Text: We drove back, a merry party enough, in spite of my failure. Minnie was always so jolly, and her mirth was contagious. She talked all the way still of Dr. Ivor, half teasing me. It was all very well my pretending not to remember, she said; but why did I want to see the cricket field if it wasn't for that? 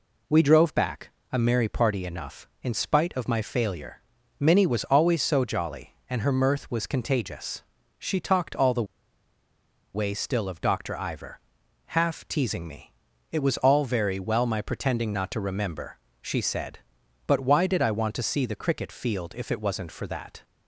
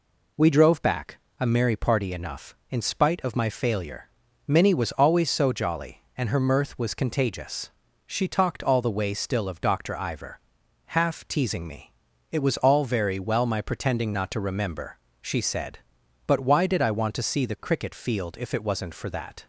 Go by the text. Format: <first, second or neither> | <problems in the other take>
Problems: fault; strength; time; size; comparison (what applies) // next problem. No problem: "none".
second | pauses between "the" and "way"; at 8.8 s; 1.1 s long